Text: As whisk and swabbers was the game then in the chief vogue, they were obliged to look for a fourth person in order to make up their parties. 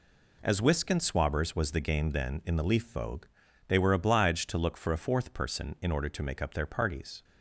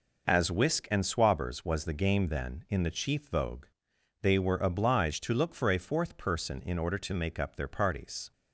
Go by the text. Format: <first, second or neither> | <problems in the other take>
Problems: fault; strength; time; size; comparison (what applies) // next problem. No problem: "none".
second | says "leaf" for "chief"; at 2.6 s